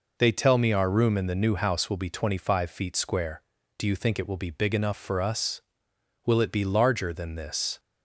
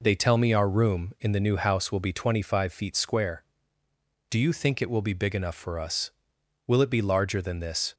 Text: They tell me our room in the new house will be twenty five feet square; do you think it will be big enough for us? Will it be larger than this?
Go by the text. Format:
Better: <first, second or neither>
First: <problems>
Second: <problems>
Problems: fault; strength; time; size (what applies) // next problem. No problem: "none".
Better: neither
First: none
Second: none